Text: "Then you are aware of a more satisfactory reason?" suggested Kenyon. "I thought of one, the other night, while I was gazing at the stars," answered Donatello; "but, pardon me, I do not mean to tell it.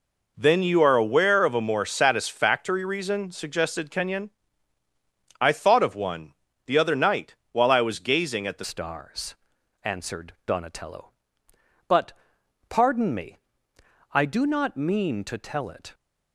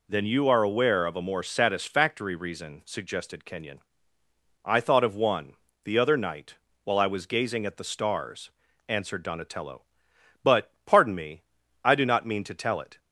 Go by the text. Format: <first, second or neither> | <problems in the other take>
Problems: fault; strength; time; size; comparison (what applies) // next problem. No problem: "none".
second | changes voice at "stars"; from 8.6 s on; 7.3 s long